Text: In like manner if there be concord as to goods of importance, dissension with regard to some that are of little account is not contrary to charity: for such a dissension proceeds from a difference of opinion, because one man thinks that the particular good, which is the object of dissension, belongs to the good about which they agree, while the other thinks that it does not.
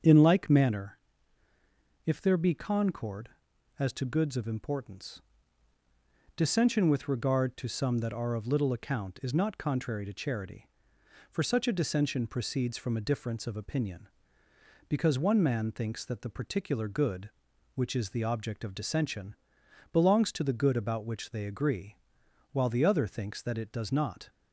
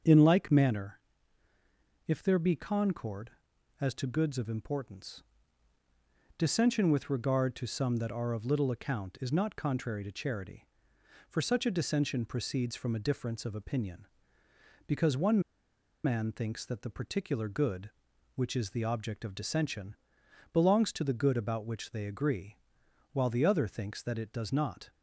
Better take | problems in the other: first | starts louder than the rest; strong; until 2.1 s; 7 dB; strong in the first // pauses between "manner" and "if"; at 1.0 s; 1.0 s long; also in the first // pauses between "one" and "man"; noticeable; at 15.4 s; 0.64 s long

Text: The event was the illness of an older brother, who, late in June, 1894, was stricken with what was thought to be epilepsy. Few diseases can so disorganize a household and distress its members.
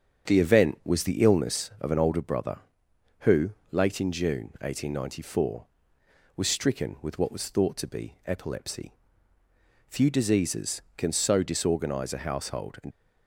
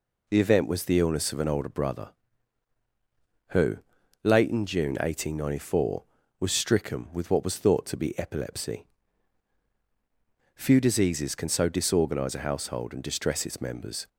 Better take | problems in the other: second | starts louder than the rest; strong; until 1.2 s; 7 dB // stops before "distress its members"; at 12.9 s

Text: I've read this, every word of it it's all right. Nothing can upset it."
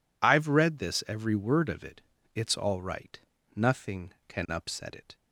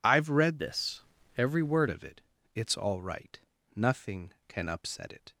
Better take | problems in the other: first | changes voice from "this" to "word"; from 0.5 to 1.8 s; 1.3 s long // pauses between "it" and "it's"; slight; at 2.2 s; 0.34 s long; slight in the first

